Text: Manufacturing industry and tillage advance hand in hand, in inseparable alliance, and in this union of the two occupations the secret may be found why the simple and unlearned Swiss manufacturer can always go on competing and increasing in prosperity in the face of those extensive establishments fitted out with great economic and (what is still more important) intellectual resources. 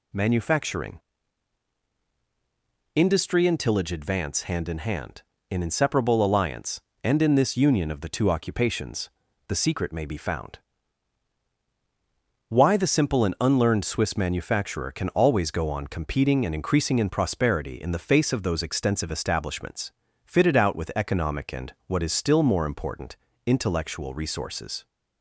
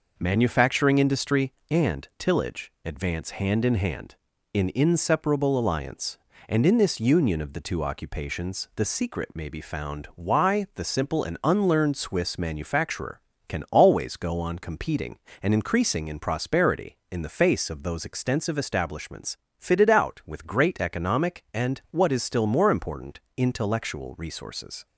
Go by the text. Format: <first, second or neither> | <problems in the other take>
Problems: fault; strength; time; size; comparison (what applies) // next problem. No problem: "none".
second | pauses between "Manufacturing" and "industry"; strong; at 0.9 s; 1.9 s long // pauses between "occupations" and "the"; at 9.0 s; 0.38 s long // pauses between "found" and "why"; strong; at 10.5 s; 1.9 s long // pauses between "establishments" and "fitted"; slight; at 19.9 s; 0.34 s long; slight in the second // skips "great"; at 20.9 s